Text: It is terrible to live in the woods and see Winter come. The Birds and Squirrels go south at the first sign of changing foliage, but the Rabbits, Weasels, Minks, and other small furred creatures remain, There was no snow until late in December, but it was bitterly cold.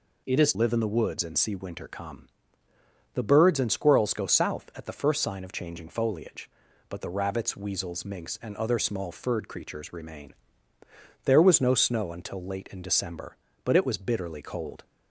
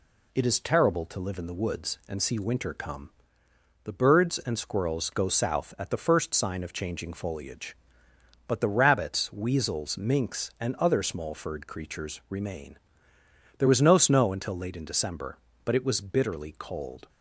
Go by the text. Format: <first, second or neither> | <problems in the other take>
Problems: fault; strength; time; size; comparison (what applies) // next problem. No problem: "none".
second | skips "terrible to"; at 0.5 s